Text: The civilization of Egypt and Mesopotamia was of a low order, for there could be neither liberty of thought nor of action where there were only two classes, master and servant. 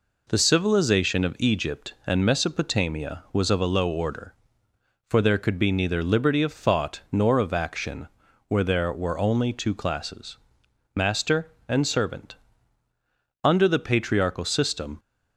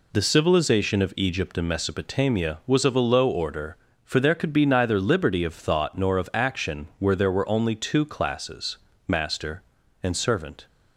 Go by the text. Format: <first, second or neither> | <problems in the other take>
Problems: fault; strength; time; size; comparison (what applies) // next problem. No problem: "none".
second | pauses between "action" and "where"; at 8.0 s; 0.40 s long // goes on to say "Under the Patriarchal system"; from 13.4 s on; 1.5 s long